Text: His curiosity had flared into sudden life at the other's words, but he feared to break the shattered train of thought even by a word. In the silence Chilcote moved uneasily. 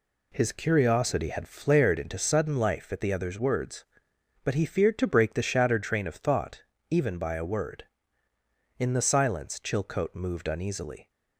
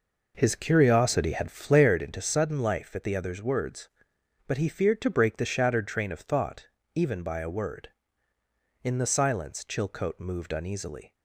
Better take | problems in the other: first | starts louder than the rest; noticeable; until 2.0 s; 5 dB // pauses between "thought" and "even"; slight; at 6.6 s; 0.28 s long; slight in the first

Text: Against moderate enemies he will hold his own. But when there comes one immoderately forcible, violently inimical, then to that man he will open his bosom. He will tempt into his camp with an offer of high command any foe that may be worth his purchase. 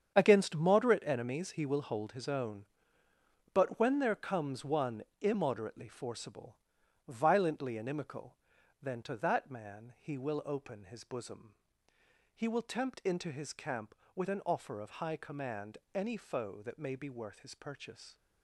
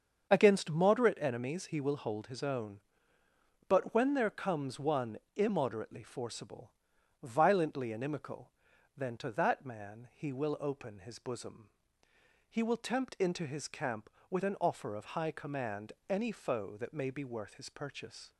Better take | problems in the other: second | gets quieter; strong; throughout; 11 dB // starts louder than the rest; strong; until 1.1 s; 8 dB; also in the second // pauses between "one" and "immoderately"; slight; at 5.0 s; 0.18 s long; slight in the second // pauses between "command" and "any"; slight; at 15.7 s; 0.16 s long; slight in the second

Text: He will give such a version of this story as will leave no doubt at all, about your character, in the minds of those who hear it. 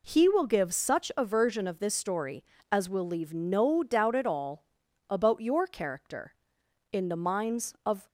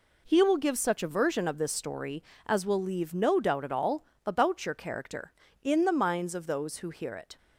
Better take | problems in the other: second | stops before "those who hear it"; at 8.0 s

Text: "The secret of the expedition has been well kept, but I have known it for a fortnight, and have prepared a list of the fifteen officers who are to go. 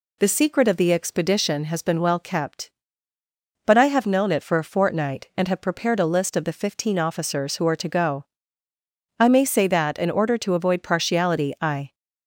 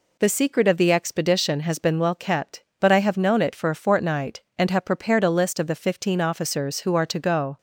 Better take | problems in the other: second | goes on to say "I may say that in order to avoid partiality I"; strong; from 9.1 s on; 2.7 s long

